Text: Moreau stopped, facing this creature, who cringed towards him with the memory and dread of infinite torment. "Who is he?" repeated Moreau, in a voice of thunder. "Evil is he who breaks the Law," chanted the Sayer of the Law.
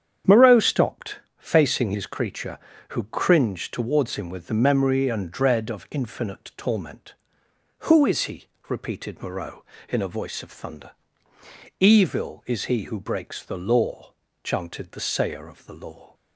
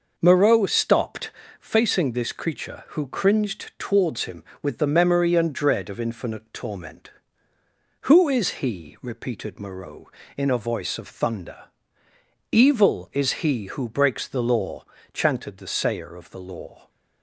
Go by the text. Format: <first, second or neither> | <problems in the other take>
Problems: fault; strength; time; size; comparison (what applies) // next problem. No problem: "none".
second | starts louder than the rest; strong; until 1.4 s; 8.5 dB // says "his" for "this"; at 1.9 s